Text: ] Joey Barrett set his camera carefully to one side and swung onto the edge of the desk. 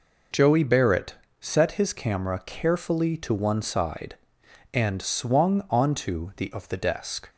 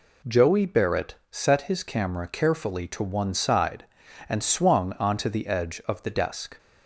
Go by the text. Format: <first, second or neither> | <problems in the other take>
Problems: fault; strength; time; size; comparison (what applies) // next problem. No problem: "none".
second | pauses between "Barrett" and "set"; slight; at 1.1 s; 0.26 s long; slight in the second // skips "edge"; at 6.5 s